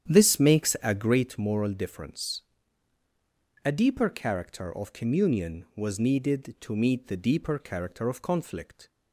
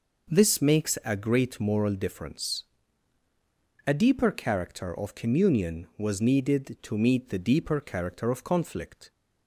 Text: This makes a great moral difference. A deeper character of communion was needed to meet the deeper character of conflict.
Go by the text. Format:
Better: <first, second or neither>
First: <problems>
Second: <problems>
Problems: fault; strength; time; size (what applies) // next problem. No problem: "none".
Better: second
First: starts louder than the rest; strong; until 1.4 s; 9.5 dB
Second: none